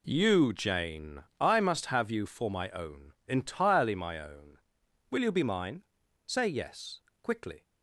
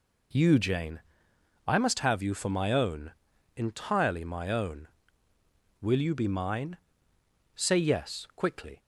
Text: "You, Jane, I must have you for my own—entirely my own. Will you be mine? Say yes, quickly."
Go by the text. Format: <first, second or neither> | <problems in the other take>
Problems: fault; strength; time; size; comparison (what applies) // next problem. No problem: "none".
neither | none